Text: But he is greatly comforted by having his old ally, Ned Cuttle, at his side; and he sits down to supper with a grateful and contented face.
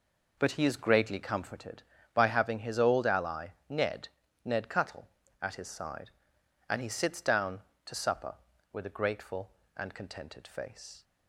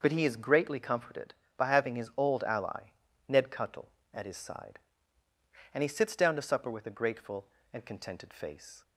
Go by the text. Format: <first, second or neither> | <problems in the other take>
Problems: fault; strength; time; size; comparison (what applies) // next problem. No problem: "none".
second | says "Ned" twice; at 4.4 s